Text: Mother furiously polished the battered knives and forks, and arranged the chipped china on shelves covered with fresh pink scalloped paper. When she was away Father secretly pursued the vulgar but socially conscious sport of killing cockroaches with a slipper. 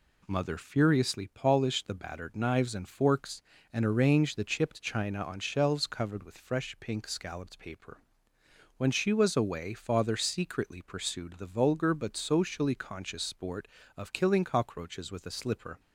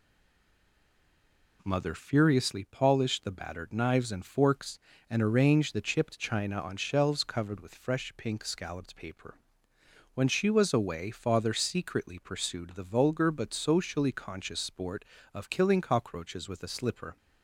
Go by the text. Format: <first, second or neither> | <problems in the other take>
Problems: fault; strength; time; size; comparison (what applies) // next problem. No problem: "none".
first | stays silent before the first word; noticeable; until 1.6 s; 1.6 s long